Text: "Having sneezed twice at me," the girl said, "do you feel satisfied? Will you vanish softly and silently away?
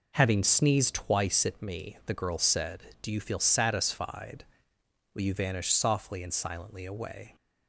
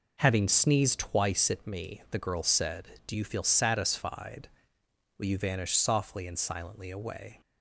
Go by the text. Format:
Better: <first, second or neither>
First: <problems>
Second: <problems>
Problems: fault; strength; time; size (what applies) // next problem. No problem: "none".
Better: neither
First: none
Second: none